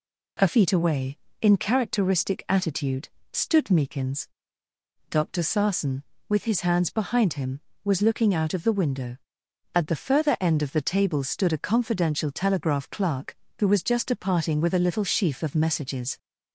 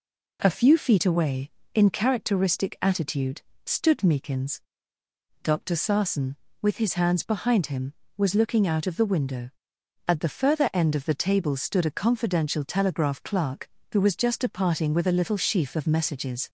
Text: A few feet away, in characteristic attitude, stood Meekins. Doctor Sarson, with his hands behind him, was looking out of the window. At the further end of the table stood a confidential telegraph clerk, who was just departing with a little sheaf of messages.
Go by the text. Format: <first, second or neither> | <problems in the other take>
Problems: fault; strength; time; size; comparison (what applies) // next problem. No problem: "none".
second | skips "few"; at 0.4 s